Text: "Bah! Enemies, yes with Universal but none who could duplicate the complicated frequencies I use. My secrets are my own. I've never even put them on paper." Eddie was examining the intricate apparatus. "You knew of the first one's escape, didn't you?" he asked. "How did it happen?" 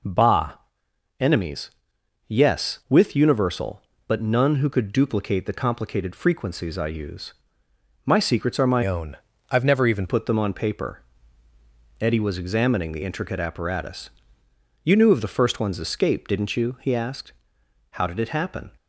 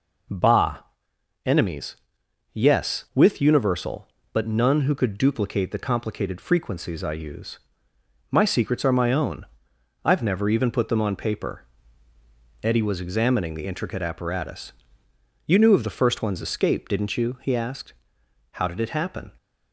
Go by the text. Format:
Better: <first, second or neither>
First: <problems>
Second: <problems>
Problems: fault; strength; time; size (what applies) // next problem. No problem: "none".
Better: second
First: changes voice from "own" to "even"; from 8.8 to 10.0 s; 1.2 s long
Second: none